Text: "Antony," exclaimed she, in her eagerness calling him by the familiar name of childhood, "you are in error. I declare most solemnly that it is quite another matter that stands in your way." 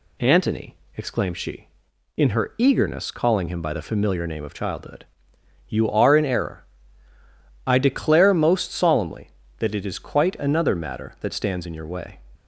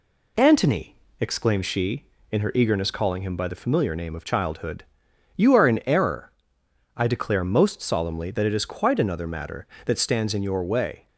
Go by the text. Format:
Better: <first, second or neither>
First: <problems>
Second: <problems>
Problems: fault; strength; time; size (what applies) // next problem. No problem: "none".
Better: neither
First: none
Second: none